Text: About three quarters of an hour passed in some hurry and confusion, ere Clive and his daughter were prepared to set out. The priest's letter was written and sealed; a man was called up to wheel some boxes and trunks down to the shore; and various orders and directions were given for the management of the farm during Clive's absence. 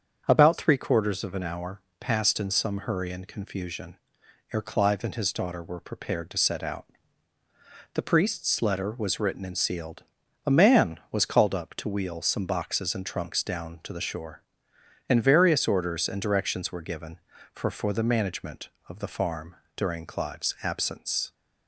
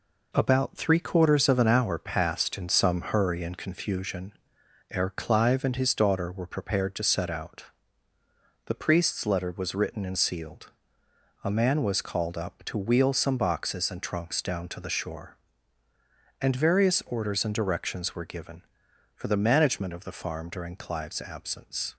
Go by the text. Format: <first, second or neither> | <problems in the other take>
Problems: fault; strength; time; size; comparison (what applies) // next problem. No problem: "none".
second | starts louder than the rest; strong; until 1.3 s; 7 dB // pauses between "hour" and "passed"; slight; at 1.8 s; 0.18 s long // says "for" twice; at 17.6 s // pauses between "farm" and "during"; slight; at 19.5 s; 0.18 s long